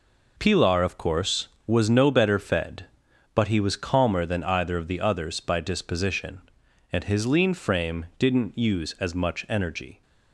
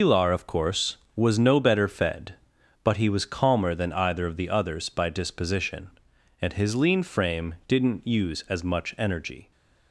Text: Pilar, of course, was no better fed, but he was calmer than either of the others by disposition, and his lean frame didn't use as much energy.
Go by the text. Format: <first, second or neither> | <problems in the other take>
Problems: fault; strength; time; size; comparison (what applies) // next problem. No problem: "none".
first | loses the start of "Pilar"; at 0.0 s; 135 ms